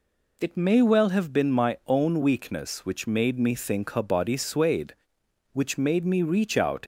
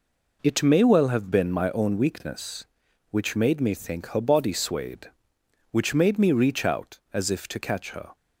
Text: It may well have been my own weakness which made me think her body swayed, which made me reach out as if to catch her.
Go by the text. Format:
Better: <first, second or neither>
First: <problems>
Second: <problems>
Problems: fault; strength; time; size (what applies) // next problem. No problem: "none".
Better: second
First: stops before "as if to catch her"; at 6.8 s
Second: none